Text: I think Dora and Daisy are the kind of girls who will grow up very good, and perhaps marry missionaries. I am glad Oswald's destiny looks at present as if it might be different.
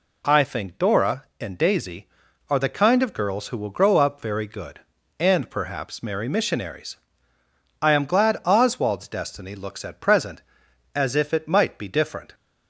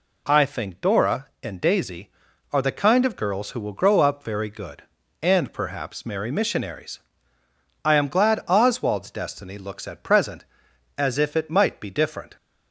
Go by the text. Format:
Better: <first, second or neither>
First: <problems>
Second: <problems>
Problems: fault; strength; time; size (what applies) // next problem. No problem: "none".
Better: neither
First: none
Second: none